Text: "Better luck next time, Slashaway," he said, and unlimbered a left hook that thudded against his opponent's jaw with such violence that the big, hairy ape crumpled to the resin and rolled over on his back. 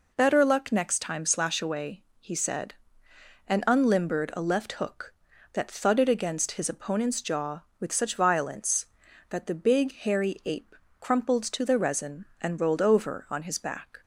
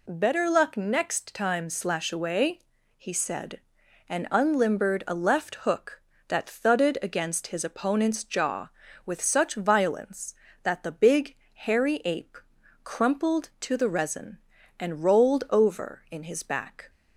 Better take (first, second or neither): first